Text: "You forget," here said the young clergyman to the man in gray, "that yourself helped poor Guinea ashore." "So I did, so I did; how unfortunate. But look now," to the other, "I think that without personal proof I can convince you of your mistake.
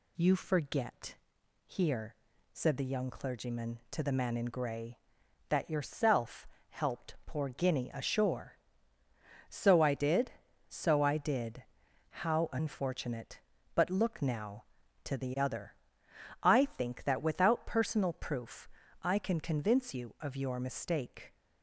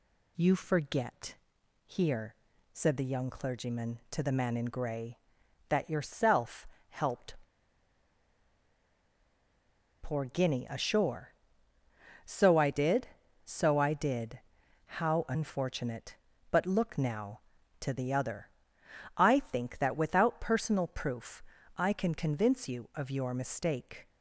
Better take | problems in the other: first | pauses between "here" and "said"; at 2.3 s; 0.38 s long; also in the first // pauses between "yourself" and "helped"; slight; at 6.6 s; 0.22 s long; slight in the first // pauses between "helped" and "poor"; strong; at 7.3 s; 2.6 s long // pauses between "proof" and "I"; slight; at 21.4 s; 0.32 s long; slight in the first

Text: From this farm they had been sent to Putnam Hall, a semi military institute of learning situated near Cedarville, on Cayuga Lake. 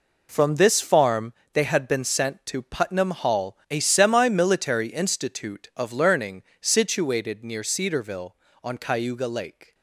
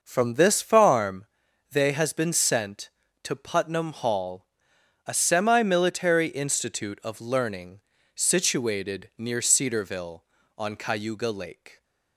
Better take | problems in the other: first | pauses between "farm" and "they"; at 1.2 s; 0.44 s long; slight in the first // says "has" for "had"; at 1.9 s // pauses between "learning" and "situated"; slight; at 7.8 s; 0.34 s long; slight in the first

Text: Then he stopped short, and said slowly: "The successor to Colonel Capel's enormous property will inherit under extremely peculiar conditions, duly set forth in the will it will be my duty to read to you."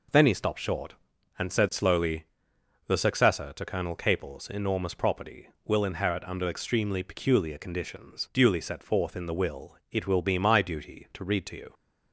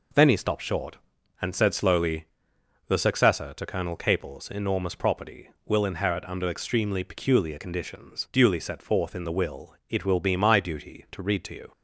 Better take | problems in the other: neither | none

